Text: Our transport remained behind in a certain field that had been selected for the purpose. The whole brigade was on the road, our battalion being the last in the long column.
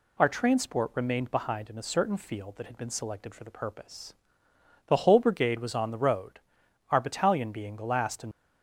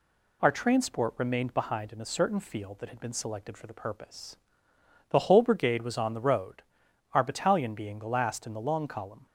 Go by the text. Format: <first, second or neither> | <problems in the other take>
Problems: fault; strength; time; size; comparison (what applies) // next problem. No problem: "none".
second | stops before "the long column"; at 8.3 s